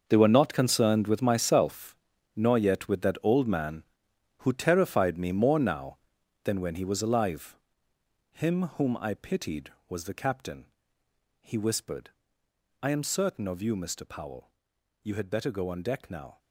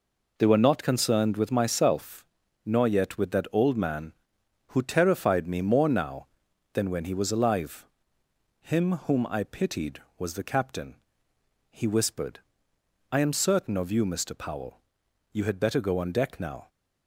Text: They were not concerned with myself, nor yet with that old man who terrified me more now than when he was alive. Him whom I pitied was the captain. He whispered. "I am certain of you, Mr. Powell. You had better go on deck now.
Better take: second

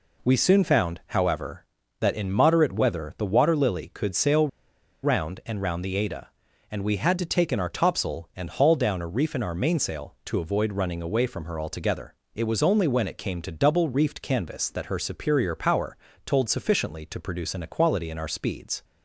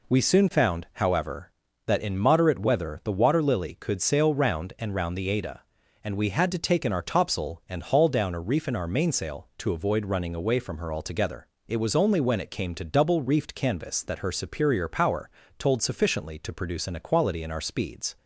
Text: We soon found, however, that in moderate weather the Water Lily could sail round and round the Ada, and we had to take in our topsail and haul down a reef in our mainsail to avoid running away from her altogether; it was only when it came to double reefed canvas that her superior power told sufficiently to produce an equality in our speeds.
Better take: second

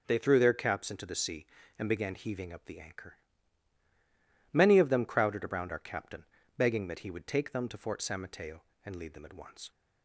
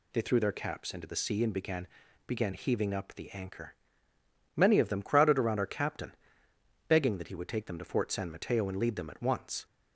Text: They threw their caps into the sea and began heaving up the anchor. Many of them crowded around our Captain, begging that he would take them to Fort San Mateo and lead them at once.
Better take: first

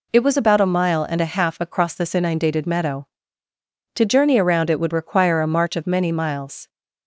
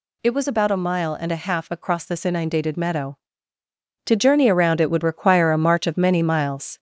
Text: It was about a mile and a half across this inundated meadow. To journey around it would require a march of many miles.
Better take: first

